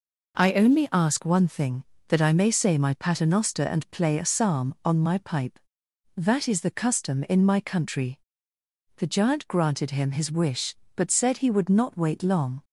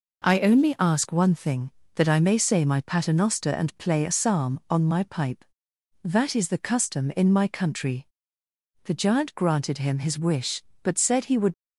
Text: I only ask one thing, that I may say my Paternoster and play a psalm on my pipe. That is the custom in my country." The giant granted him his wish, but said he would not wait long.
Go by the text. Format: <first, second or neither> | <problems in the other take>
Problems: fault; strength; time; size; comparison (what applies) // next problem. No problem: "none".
first | stops before "not wait long"; at 11.5 s